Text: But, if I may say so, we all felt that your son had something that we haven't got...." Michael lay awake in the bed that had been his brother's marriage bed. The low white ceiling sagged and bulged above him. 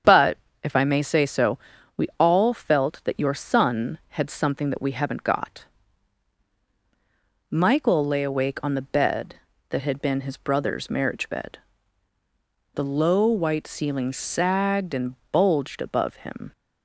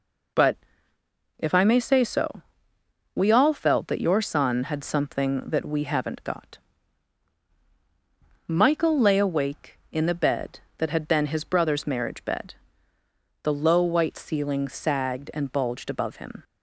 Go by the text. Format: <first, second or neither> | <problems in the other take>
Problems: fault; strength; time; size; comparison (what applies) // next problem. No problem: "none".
second | starts louder than the rest; strong; until 1.3 s; 8 dB // says "on" for "in"; at 8.6 s // pauses between "and" and "bulged"; slight; at 15.1 s; 0.16 s long